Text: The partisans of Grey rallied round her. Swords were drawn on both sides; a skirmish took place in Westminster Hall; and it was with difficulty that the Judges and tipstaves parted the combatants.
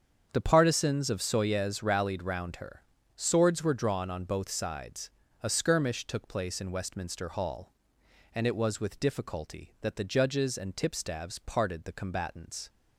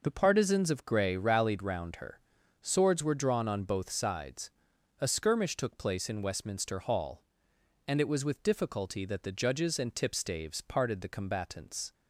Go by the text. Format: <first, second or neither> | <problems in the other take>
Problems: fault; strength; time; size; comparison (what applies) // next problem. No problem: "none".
second | starts louder than the rest; strong; until 1.3 s; 7.5 dB // says "Soyez" for "Grey"; at 1.2 s